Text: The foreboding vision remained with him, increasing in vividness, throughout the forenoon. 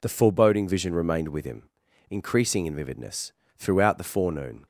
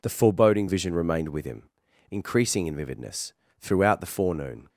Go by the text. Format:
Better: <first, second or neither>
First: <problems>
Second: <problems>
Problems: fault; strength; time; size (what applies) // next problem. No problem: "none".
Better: neither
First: none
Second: none